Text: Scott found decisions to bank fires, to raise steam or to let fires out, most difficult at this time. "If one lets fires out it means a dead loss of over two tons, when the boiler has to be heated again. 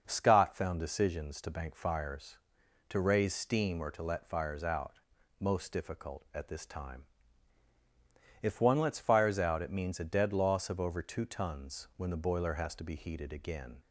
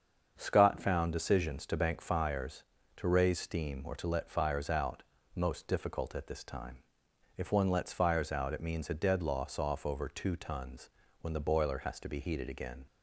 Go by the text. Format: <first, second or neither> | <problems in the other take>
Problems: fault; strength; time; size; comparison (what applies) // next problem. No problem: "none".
first | starts louder than the rest; until 1.3 s; 7 dB // says "off" for "of"; at 9.5 s